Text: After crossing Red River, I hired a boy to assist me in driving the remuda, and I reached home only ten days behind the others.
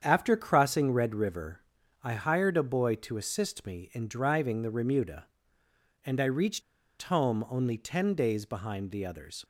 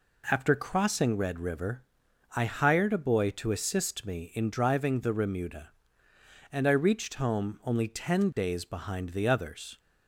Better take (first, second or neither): second